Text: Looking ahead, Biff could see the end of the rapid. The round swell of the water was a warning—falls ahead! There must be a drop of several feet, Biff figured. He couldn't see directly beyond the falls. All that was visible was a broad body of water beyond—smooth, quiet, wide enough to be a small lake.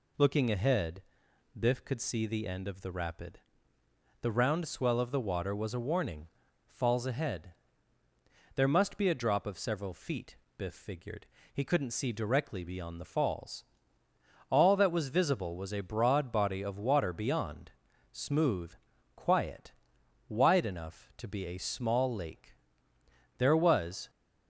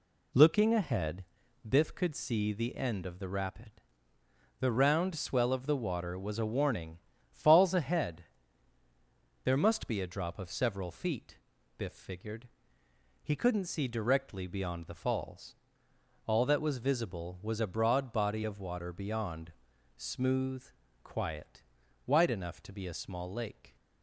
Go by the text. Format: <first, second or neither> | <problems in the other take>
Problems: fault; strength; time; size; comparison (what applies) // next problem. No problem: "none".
second | goes on to say "There was"; noticeable; from 23.3 s on; 0.72 s long